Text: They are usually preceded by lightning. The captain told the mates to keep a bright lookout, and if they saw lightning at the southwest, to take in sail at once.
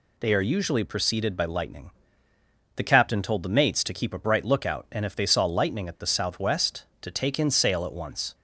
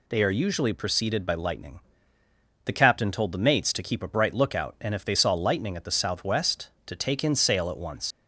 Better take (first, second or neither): first